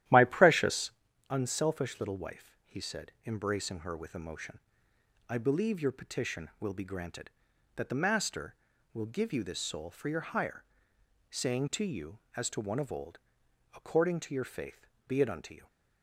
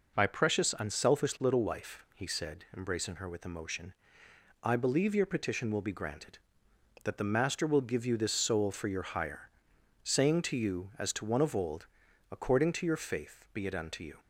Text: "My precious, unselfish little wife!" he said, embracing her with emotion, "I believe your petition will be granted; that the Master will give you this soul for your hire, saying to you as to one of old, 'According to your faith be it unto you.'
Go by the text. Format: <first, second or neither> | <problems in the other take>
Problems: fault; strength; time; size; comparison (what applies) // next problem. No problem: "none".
second | starts louder than the rest; strong; until 1.1 s; 12.5 dB // pauses between "faith" and "be"; slight; at 14.8 s; 0.22 s long